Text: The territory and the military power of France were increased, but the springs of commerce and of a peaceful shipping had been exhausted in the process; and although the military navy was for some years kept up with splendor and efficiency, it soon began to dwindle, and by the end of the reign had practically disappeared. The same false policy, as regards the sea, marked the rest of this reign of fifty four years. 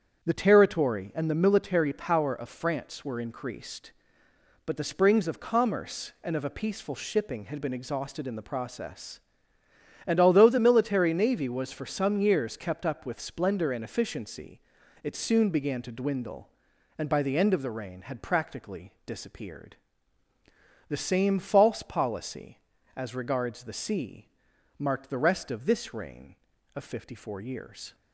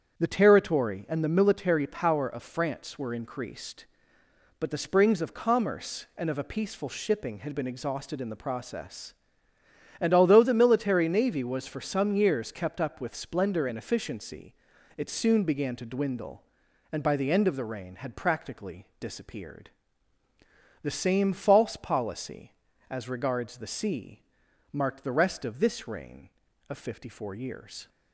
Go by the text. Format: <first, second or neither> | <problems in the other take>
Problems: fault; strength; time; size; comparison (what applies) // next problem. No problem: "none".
neither | starts louder than the rest; strong; the same in both // pauses between "practically" and "disappeared"; slight; the same in both